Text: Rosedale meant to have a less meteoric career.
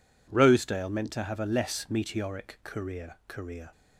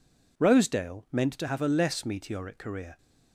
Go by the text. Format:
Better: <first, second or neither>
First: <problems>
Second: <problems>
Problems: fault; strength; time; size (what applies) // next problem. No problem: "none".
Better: second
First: says "career" twice; at 3.2 s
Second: none